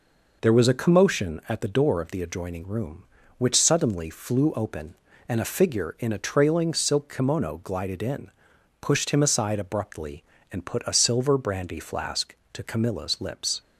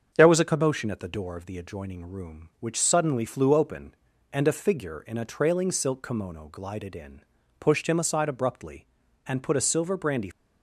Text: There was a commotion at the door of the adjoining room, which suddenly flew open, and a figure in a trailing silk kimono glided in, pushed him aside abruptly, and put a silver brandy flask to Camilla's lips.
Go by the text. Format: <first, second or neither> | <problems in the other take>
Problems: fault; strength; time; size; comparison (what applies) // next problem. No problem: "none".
first | starts louder than the rest; until 1.1 s; 7 dB // stops before "flask to Camilla's lips"; at 10.3 s